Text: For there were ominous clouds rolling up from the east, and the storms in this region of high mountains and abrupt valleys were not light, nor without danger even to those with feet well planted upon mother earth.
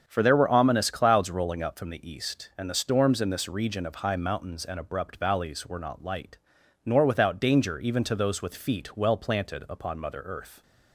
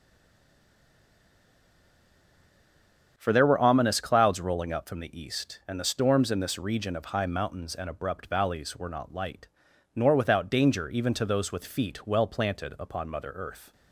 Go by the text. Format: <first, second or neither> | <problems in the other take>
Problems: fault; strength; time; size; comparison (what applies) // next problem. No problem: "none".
first | stays silent before the first word; strong; until 3.1 s; 3.1 s long // starts louder than the rest; strong; until 4.1 s; 7 dB; strong in the first